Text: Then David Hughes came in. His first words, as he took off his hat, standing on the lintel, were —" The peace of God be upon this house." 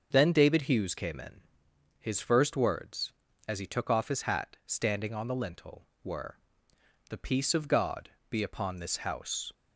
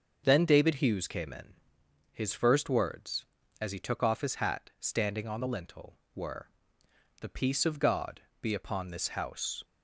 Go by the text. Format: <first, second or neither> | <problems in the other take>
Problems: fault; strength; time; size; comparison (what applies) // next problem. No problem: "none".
neither | starts louder than the rest; the same in both // pauses between "God" and "be"; slight; the same in both